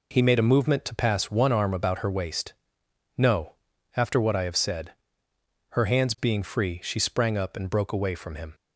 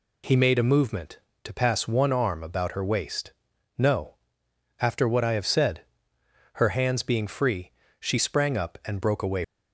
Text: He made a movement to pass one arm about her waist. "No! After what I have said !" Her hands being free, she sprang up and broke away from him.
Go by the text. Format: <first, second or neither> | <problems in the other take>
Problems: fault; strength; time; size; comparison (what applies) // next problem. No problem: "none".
first | stops before "from him"; at 9.4 s